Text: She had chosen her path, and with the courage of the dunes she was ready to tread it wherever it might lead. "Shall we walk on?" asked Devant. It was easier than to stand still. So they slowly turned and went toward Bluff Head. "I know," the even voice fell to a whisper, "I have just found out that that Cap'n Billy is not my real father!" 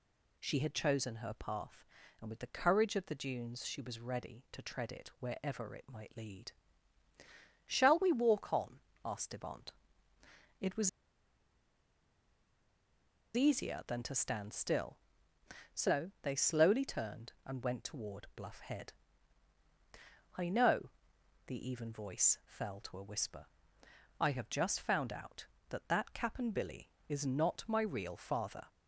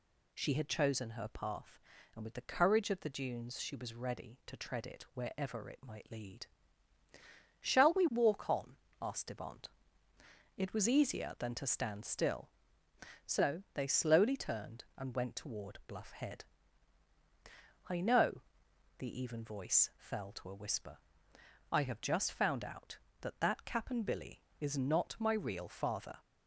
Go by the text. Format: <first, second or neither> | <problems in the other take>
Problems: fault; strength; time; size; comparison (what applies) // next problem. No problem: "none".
second | pauses between "was" and "easier"; strong; at 10.8 s; 2.4 s long